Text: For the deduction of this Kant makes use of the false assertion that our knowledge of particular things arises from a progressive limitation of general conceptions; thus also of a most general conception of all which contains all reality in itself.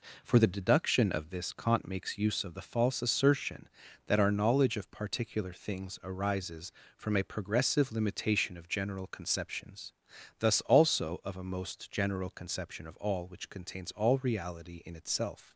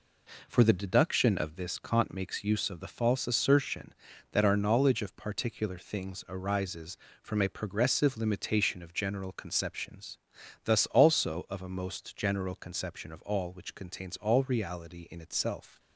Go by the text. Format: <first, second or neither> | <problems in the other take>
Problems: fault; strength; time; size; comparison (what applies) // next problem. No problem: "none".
neither | none